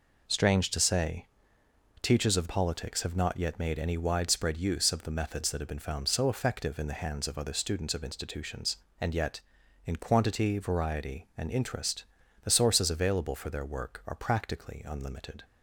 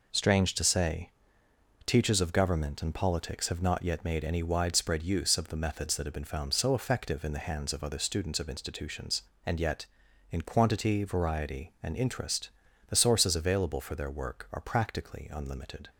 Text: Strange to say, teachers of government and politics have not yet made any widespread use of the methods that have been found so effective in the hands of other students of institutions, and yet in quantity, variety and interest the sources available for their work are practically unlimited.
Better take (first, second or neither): second